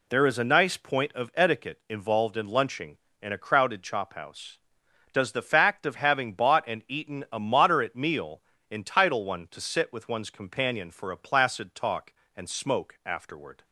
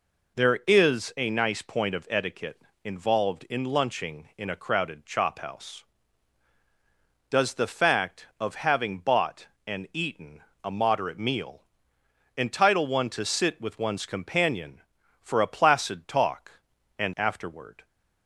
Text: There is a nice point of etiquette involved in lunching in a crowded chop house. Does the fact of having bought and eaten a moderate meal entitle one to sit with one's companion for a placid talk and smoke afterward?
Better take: first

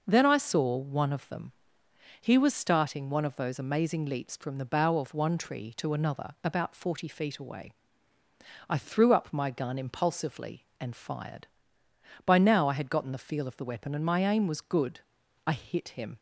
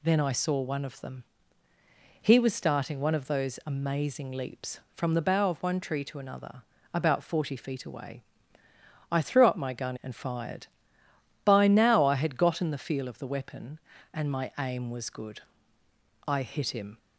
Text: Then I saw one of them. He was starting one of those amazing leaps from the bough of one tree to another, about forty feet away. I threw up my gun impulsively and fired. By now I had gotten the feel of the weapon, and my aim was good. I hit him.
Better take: first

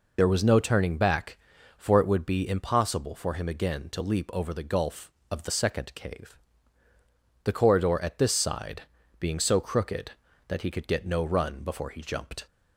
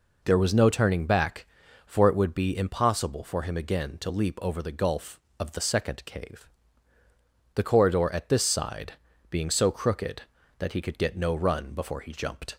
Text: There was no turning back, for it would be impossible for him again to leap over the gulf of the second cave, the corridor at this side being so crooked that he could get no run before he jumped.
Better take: second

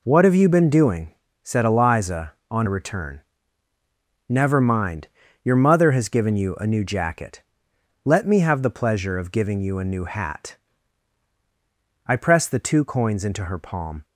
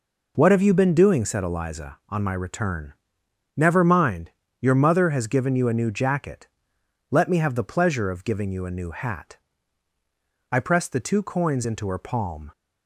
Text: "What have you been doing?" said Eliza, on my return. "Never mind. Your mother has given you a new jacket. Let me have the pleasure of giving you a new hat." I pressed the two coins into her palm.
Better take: second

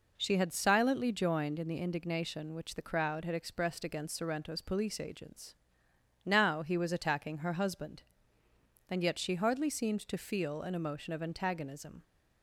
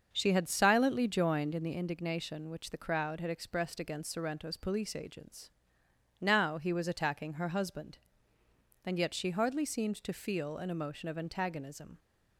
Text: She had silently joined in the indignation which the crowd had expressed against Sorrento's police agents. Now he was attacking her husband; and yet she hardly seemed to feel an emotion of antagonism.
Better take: first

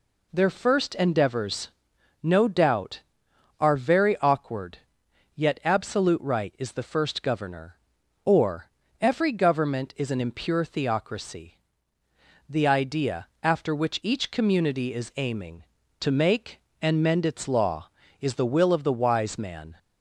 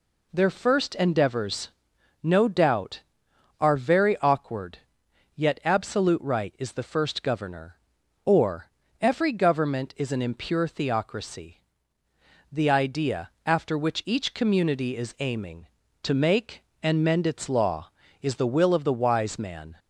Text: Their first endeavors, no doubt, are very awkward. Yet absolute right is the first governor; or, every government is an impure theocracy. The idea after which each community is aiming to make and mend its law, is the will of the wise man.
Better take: neither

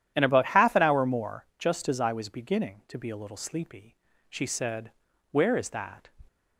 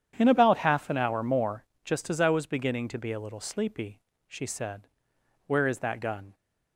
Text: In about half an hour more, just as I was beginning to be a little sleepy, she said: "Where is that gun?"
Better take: second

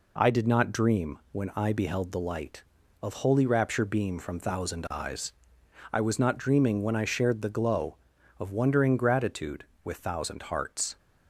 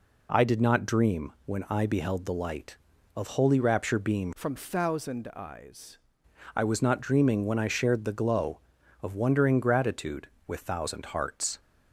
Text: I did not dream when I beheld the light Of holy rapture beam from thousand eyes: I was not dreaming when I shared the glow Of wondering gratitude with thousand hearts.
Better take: first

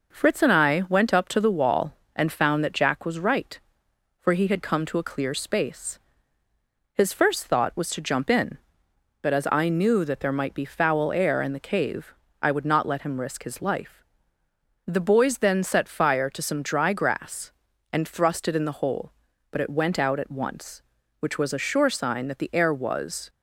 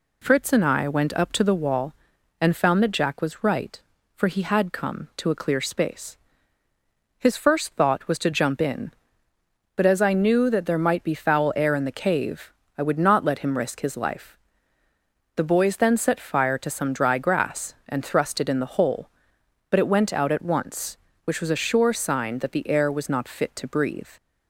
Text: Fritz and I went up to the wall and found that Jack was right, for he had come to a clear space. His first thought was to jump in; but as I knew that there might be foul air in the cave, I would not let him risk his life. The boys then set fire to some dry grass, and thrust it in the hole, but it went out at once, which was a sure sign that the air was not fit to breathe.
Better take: second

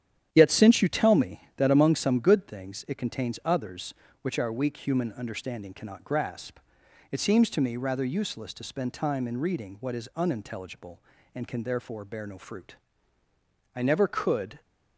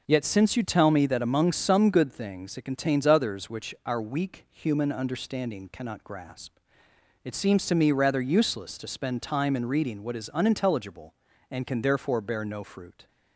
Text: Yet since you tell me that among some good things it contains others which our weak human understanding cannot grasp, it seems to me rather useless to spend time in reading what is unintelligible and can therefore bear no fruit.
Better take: second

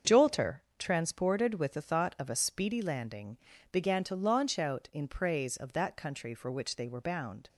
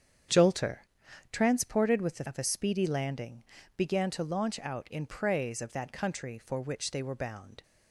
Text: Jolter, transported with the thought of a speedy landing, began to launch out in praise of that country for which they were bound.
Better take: first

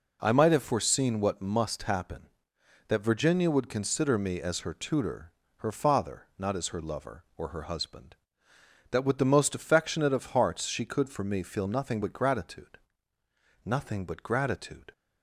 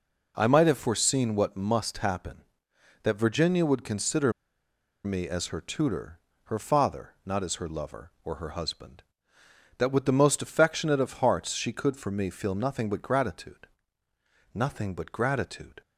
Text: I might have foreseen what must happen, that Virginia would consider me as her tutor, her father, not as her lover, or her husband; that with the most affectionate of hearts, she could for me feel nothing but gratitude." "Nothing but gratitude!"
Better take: first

